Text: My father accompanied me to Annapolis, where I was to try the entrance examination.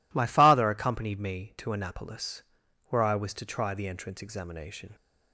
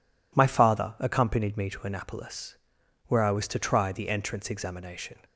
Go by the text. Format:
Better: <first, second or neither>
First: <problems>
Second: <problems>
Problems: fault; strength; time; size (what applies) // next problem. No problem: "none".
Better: neither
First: none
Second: none